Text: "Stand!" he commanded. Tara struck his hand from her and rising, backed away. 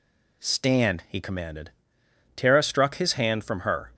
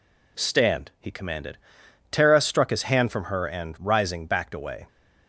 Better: second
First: stops before "and rising backed away"; at 3.9 s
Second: none

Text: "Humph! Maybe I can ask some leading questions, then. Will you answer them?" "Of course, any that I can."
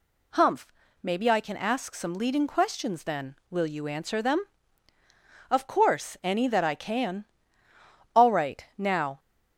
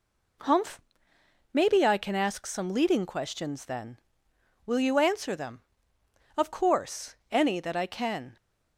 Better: second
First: goes on to say "All right Now"; noticeable; from 8.1 s on; 1.0 s long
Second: none

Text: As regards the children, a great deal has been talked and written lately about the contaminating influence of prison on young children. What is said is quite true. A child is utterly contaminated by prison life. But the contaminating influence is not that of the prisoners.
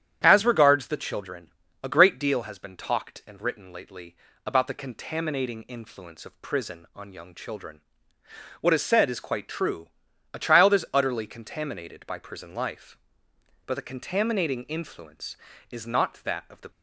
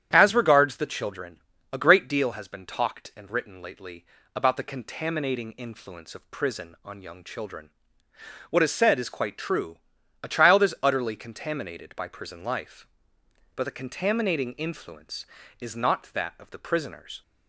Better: second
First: starts louder than the rest; strong; until 1.2 s; 9.5 dB // pauses between "lately" and "about"; slight; at 4.1 s; 0.32 s long // stops before "prisoners"; at 16.7 s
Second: starts louder than the rest; strong; until 1.1 s; 9.5 dB // pauses between "lately" and "about"; slight; at 4.0 s; 0.32 s long

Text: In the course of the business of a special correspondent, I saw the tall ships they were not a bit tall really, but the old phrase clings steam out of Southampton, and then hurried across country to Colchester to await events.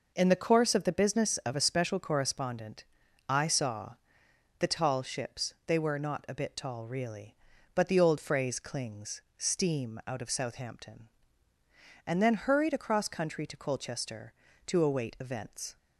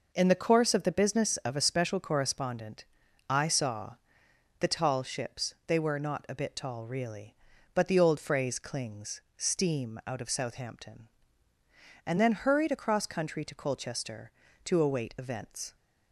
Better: neither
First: pauses between "saw" and "the"; noticeable; at 3.9 s; 0.64 s long // pauses between "clings" and "steam"; slight; at 9.2 s; 0.16 s long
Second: pauses between "saw" and "the"; noticeable; at 3.9 s; 0.64 s long // pauses between "clings" and "steam"; slight; at 9.2 s; 0.16 s long

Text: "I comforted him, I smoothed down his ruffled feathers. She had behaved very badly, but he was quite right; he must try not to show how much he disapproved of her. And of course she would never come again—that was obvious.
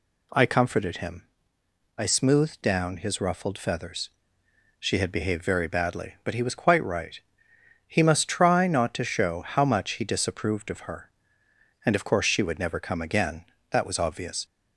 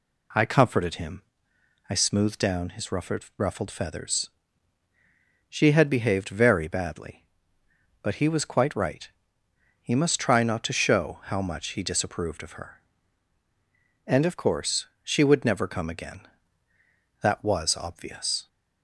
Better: first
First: none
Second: says "ruffled" twice; at 3.3 s // pauses between "course" and "she"; slight; at 14.8 s; 0.16 s long

